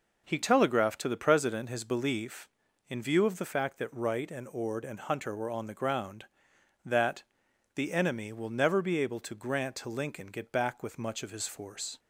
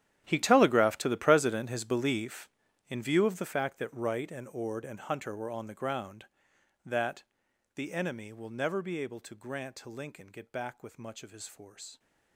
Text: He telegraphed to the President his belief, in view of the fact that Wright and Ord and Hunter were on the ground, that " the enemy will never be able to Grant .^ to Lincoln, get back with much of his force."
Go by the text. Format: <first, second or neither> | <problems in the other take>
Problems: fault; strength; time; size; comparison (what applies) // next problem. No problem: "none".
first | gets quieter; strong; throughout; 18.5 dB